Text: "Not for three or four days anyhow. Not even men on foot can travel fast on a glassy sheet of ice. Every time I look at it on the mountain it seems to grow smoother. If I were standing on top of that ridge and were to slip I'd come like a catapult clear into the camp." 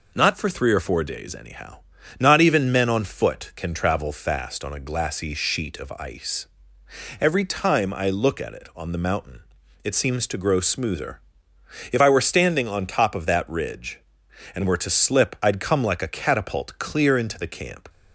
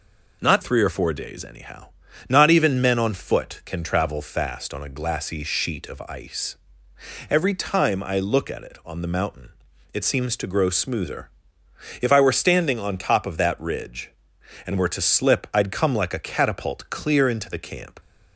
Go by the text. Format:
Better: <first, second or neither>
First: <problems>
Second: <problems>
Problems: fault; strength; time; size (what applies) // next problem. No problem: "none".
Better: first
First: pauses between "mountain" and "it"; at 9.4 s; 0.44 s long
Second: skips "for"; at 0.6 s // pauses between "mountain" and "it"; at 9.5 s; 0.44 s long